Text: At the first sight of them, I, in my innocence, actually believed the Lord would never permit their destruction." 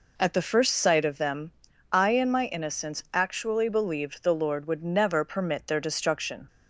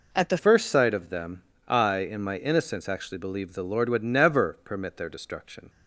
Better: first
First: none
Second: changes voice at "first"; from 0.3 s on; 5.3 s long

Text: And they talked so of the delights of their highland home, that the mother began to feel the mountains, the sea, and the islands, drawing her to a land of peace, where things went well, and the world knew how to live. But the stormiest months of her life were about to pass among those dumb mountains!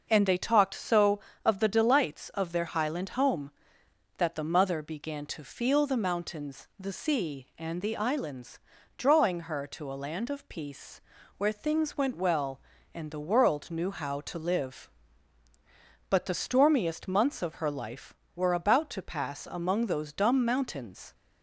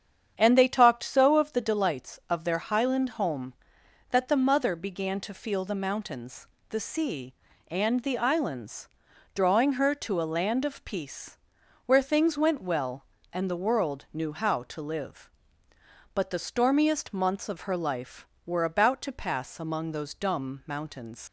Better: first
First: starts louder than the rest; noticeable; until 1.1 s; 6 dB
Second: starts louder than the rest; strong; until 1.3 s; 8 dB // leaves "mountains" unfinished; at 21.2 s; 90 ms

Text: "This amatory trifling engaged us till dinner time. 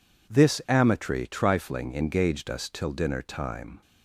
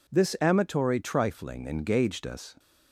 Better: first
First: none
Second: stops before "till dinner time"; at 2.5 s

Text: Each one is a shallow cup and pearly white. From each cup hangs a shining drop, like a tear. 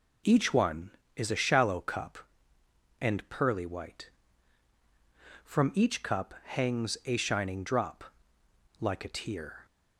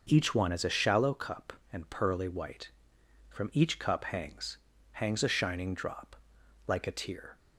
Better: first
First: none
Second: says "hangs" twice; at 4.9 s

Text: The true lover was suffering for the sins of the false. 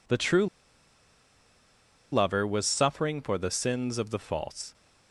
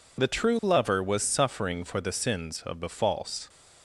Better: second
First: pauses between "true" and "lover"; strong; at 0.4 s; 1.6 s long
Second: none

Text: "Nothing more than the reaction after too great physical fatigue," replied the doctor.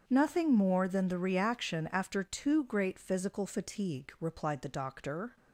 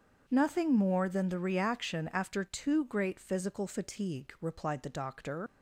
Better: first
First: starts louder than the rest; until 1.0 s; 7 dB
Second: starts louder than the rest; until 1.2 s; 7 dB // leaves "doctor" unfinished; at 5.4 s; 105 ms

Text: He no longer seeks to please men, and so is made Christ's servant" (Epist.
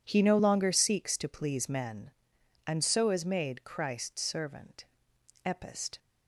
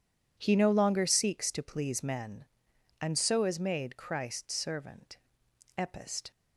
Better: neither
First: none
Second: none

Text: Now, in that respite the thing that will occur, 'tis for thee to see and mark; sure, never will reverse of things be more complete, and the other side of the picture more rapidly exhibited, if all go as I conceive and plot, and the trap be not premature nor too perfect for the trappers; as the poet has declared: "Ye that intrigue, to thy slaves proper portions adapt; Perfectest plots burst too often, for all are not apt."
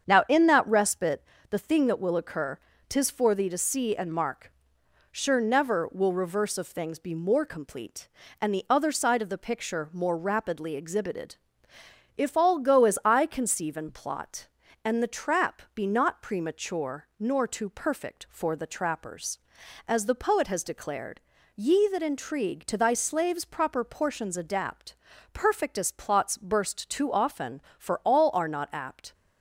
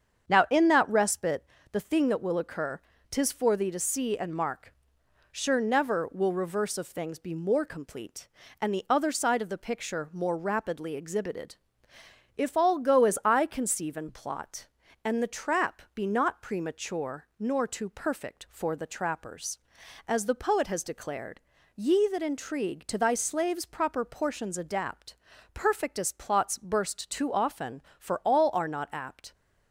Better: neither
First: starts louder than the rest; strong; until 1.0 s; 7.5 dB // pauses between "respite" and "the"; slight; at 1.2 s; 0.28 s long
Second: starts louder than the rest; strong; until 1.3 s; 7.5 dB // pauses between "respite" and "the"; slight; at 1.4 s; 0.28 s long

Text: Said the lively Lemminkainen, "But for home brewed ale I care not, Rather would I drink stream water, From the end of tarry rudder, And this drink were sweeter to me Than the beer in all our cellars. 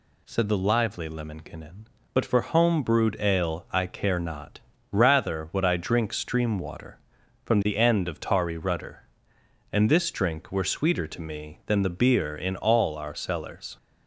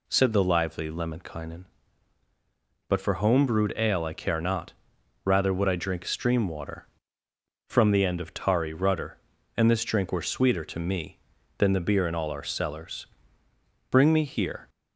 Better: first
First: none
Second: goes on to say "Bring me here"; noticeable; from 13.8 s on; 0.80 s long

